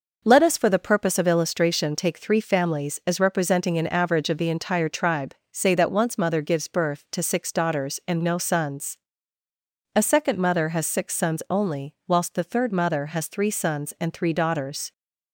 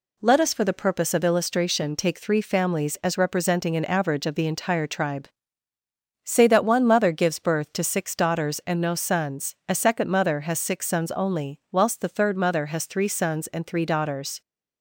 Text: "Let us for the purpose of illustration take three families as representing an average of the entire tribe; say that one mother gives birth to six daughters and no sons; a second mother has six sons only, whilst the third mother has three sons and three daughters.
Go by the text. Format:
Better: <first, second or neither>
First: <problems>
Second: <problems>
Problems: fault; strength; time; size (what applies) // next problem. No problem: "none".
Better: second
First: says "once" for "one"; at 5.8 s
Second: none